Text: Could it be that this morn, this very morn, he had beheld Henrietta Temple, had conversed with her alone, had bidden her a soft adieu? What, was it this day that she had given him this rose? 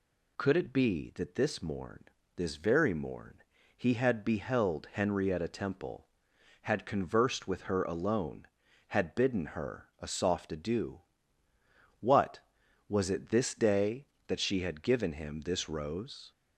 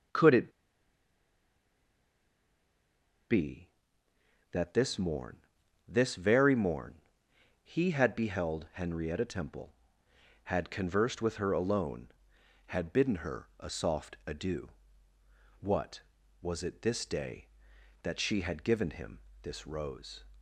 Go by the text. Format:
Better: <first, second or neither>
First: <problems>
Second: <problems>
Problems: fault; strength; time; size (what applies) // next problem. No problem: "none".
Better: first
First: none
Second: pauses between "it" and "be"; strong; at 0.4 s; 2.7 s long // pauses between "him" and "this"; slight; at 19.1 s; 0.24 s long